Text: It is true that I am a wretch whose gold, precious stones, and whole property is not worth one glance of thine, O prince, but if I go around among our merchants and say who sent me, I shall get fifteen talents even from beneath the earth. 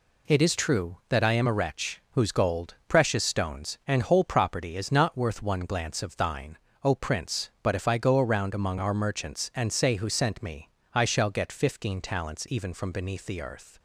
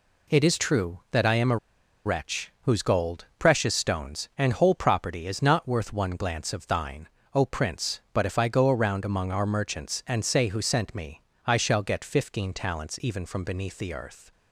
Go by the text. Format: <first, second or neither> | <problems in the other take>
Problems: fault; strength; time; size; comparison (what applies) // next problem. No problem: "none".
first | pauses between "a" and "wretch"; noticeable; at 1.5 s; 0.48 s long